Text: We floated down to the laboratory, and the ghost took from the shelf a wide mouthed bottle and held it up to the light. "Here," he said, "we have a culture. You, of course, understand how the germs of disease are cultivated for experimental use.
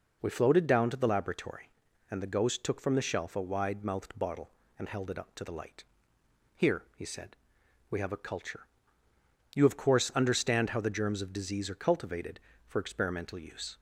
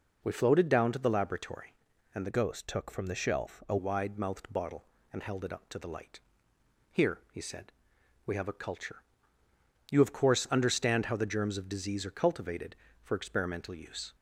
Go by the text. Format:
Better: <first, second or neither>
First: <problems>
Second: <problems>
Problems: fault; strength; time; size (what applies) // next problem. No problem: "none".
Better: first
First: none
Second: changes voice from "ghost" to "a"; from 2.3 to 3.7 s; 1.4 s long